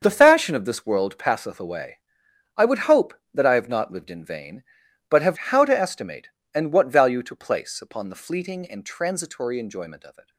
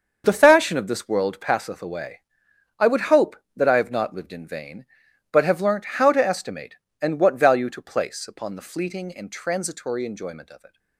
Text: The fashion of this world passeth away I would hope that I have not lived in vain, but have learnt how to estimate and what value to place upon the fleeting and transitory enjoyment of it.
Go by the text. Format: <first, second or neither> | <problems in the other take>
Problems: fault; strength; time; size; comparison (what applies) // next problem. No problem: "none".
second | starts louder than the rest; until 1.0 s; 6.5 dB; also in the second // pauses between "away" and "I"; noticeable; at 1.9 s; 0.58 s long; noticeable in the second // skips "learnt"; at 5.3 s